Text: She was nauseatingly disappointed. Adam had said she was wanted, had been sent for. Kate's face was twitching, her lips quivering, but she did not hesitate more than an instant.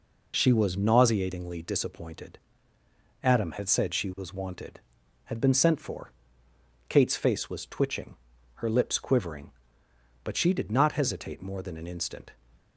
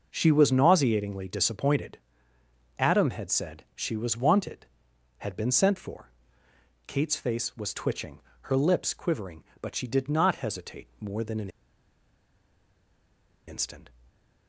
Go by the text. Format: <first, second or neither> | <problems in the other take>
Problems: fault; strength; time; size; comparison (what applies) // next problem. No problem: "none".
first | pauses between "an" and "instant"; strong; at 11.4 s; 1.9 s long // stays silent after the last word; slight; from 13.9 s on; 0.5 s long